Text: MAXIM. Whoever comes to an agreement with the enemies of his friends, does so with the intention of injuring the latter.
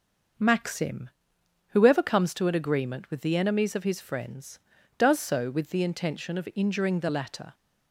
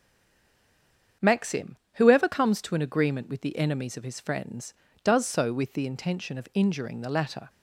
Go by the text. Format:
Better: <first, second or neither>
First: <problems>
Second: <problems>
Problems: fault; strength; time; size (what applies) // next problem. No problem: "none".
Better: first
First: starts louder than the rest; noticeable; until 1.9 s; 6 dB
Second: stays silent before the first word; noticeable; until 1.2 s; 1.2 s long // starts louder than the rest; strong; until 2.4 s; 7.5 dB